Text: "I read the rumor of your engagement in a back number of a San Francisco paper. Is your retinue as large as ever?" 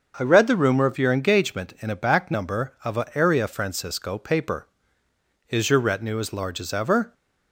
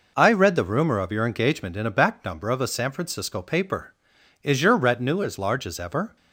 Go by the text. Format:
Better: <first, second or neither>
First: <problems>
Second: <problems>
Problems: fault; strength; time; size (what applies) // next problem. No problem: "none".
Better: second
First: starts louder than the rest; until 1.1 s; 6.5 dB // says "Area" for "San"; at 3.1 s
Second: none